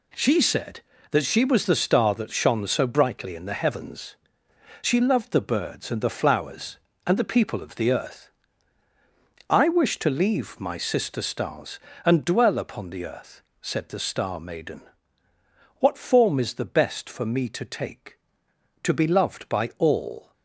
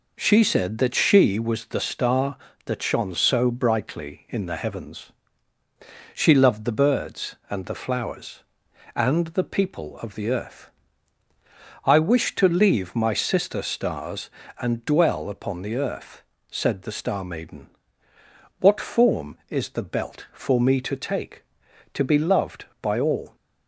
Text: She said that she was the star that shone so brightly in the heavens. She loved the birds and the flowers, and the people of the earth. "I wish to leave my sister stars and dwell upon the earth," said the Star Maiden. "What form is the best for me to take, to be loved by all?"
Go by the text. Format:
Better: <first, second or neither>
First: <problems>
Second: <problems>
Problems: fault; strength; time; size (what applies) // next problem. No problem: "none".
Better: first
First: none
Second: says "belt" for "best"; at 19.8 s